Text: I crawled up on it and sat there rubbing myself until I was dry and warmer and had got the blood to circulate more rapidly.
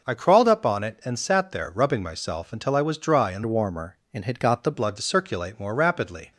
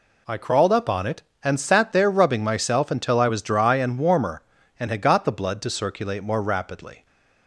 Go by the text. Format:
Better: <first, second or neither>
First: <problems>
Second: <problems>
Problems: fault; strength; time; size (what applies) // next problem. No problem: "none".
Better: second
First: changes voice from "warmer" to "the"; from 3.4 to 4.7 s; 1.3 s long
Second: none